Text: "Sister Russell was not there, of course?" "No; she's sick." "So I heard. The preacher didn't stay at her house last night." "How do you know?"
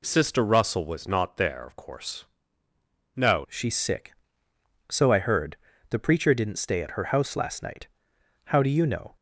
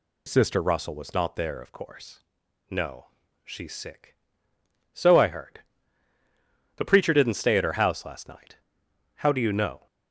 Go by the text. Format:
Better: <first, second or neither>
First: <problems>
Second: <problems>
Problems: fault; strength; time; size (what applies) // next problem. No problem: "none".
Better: second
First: changes voice at "she's"; from 3.4 s on; 5.7 s long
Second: none